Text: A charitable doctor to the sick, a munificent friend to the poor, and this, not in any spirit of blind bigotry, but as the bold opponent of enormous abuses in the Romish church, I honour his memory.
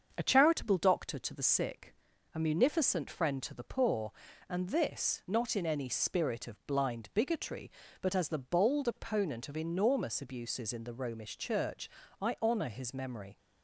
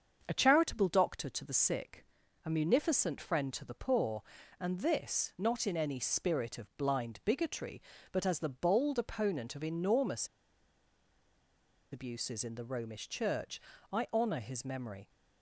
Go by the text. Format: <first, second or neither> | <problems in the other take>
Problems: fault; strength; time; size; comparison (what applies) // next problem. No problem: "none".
first | starts louder than the rest; until 1.2 s; 7 dB; also in the first // pauses between "enormous" and "abuses"; strong; at 10.2 s; 1.6 s long